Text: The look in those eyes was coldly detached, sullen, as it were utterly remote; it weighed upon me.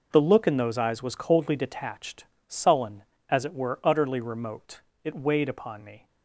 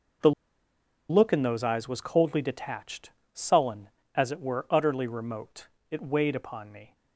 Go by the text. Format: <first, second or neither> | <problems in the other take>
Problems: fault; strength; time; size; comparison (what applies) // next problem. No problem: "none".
first | pauses between "The" and "look"; noticeable; at 0.3 s; 0.78 s long